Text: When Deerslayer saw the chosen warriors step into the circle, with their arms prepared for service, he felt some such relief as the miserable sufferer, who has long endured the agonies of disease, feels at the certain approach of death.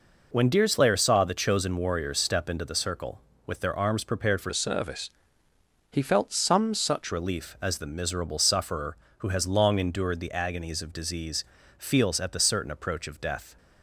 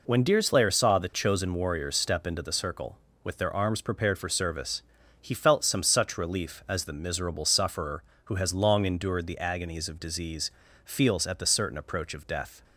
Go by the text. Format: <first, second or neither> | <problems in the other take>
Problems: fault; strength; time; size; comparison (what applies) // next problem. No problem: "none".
second | changes voice from "service" to "such"; from 4.5 to 7.1 s; 2.6 s long